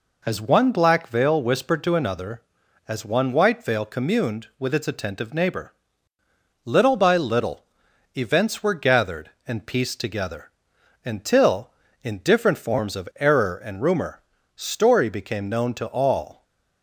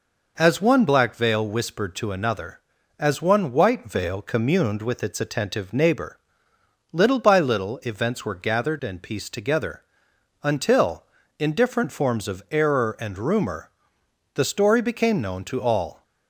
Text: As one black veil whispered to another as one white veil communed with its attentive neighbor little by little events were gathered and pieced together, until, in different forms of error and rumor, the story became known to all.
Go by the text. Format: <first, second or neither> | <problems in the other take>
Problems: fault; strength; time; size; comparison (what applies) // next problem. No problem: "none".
second | pauses between "neighbor" and "little"; noticeable; at 5.7 s; 0.90 s long; noticeable in the second // pauses between "little" and "events"; noticeable; at 7.6 s; 0.50 s long // skips "the"; at 14.3 s